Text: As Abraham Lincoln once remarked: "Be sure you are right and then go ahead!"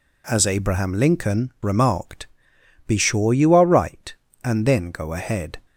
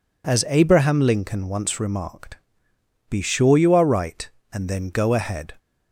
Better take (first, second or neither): second